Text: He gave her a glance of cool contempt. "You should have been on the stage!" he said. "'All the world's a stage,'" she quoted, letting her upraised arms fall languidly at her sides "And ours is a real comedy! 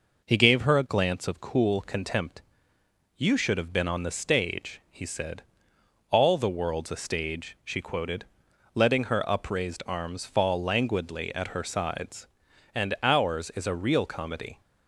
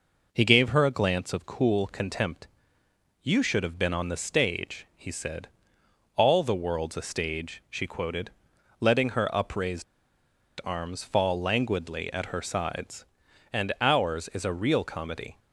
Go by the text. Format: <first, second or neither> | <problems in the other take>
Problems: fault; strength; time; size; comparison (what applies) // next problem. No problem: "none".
first | pauses between "upraised" and "arms"; noticeable; at 9.8 s; 0.79 s long